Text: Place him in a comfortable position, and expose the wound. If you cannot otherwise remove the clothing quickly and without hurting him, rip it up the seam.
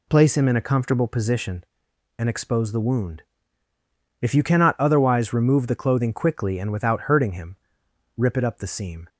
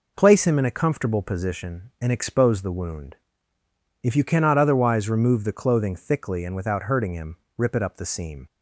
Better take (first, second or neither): first